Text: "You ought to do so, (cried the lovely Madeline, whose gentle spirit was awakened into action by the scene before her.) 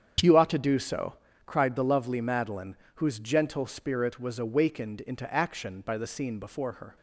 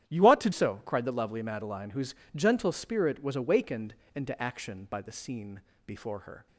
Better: first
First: starts louder than the rest; strong; until 1.5 s; 8 dB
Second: starts louder than the rest; strong; until 1.1 s; 11 dB // skips "do"; at 0.5 s // pauses between "whose" and "gentle"; slight; at 2.1 s; 0.20 s long // pauses between "awakened" and "into"; slight; at 3.9 s; 0.22 s long // pauses between "scene" and "before"; slight; at 5.6 s; 0.24 s long

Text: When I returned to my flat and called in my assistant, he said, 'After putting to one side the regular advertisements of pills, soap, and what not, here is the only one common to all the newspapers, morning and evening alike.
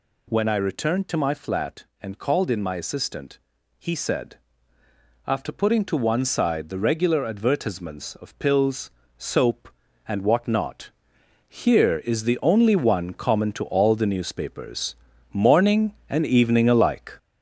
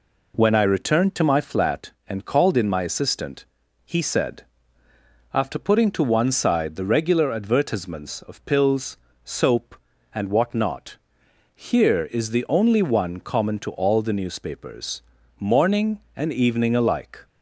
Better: second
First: gets louder; noticeable; throughout; 5 dB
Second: none

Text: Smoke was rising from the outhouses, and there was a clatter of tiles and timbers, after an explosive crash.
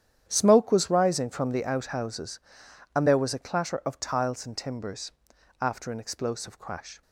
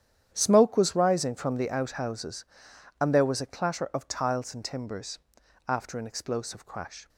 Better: neither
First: starts louder than the rest; strong; until 1.2 s; 10 dB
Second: starts louder than the rest; strong; until 1.3 s; 10 dB

